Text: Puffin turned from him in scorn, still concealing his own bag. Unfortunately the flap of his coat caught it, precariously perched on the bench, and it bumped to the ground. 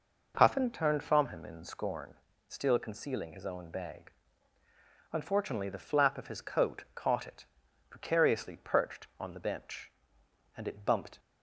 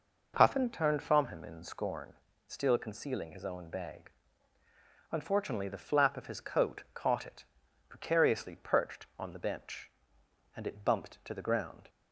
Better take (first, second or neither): second